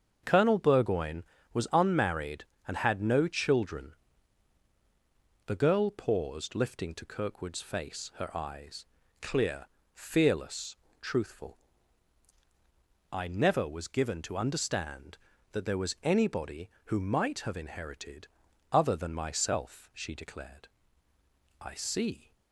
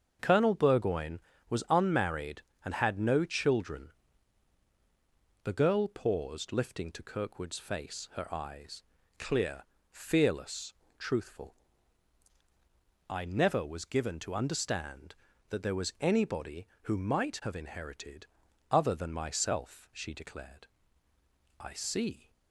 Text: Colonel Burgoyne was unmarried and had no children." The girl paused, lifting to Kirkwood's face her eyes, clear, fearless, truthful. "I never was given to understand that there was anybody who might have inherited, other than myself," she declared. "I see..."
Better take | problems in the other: neither | starts louder than the rest; the same in both

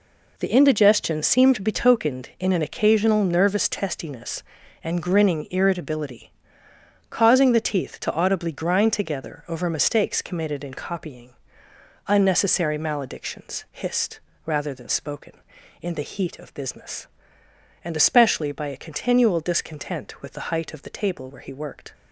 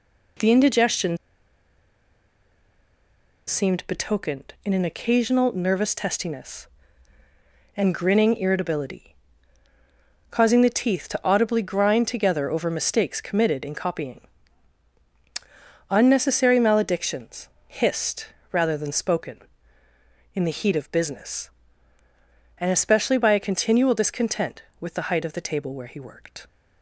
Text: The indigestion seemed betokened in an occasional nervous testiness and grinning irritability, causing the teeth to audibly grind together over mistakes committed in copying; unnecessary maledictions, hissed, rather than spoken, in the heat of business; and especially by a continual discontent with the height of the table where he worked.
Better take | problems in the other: first | pauses between "indigestion" and "seemed"; strong; at 1.1 s; 2.3 s long

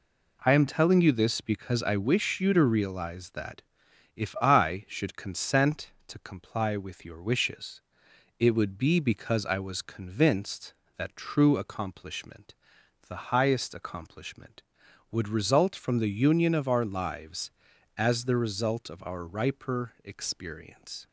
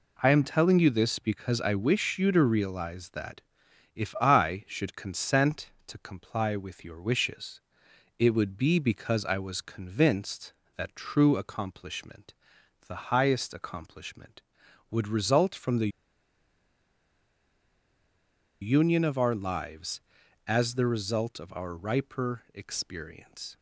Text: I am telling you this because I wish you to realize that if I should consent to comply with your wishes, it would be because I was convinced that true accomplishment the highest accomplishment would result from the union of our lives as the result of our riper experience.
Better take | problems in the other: first | pauses between "that" and "if"; noticeable; at 3.4 s; 0.52 s long; noticeable in the first // pauses between "accomplishment" and "the"; noticeable; at 12.3 s; 0.56 s long; noticeable in the first // pauses between "the" and "union"; strong; at 15.8 s; 2.7 s long

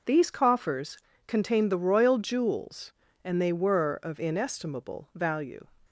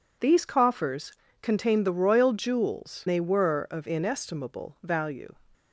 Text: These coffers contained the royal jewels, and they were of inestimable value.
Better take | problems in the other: first | pauses between "coffers" and "contained"; slight; at 1.1 s; 0.30 s long; slight in the first // skips "and"; at 3.0 s

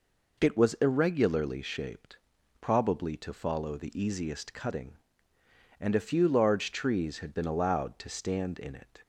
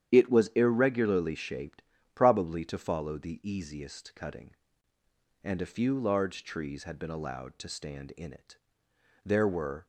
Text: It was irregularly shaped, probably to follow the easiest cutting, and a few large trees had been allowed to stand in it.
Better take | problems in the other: first | starts louder than the rest; strong; until 1.1 s; 9.5 dB // goes on to say "There were"; noticeable; from 9.2 s on; 0.62 s long

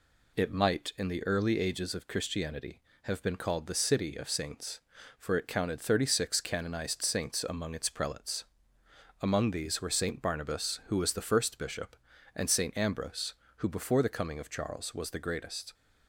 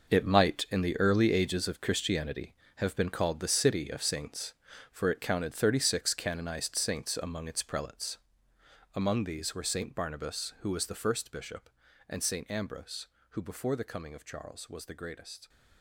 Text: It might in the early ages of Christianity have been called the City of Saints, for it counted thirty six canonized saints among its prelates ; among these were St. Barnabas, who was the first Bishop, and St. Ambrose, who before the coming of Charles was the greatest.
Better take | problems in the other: first | gets quieter; strong; throughout; 12.5 dB

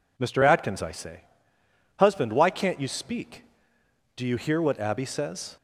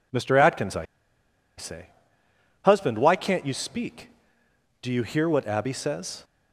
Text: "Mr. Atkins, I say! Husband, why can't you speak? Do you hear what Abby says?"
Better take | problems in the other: first | pauses between "I" and "say"; noticeable; at 0.8 s; 0.72 s long

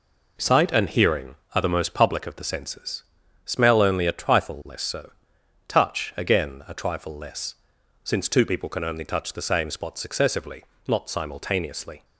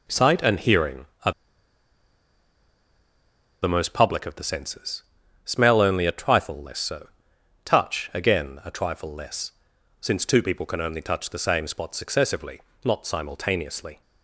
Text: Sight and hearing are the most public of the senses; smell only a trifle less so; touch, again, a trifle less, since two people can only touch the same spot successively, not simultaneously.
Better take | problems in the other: first | pauses between "are" and "the"; strong; at 1.3 s; 2.3 s long

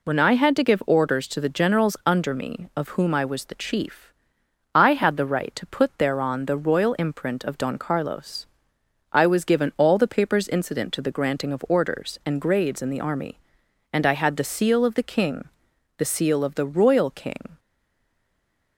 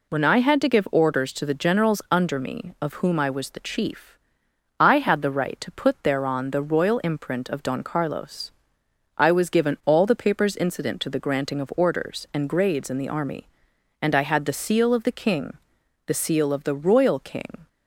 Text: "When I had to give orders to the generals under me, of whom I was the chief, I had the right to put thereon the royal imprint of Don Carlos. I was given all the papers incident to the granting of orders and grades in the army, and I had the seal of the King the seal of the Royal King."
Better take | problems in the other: second | pauses between "King" and "the"; noticeable; at 15.4 s; 0.50 s long; noticeable in the second // stays silent after the last word; noticeable; from 17.5 s on; 1.2 s long

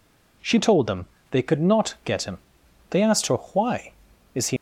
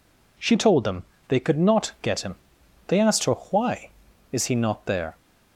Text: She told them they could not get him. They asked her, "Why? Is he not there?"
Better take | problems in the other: second | pauses between "them" and "they"; slight; at 1.0 s; 0.26 s long; slight in the second // stops before "not there"; at 4.5 s

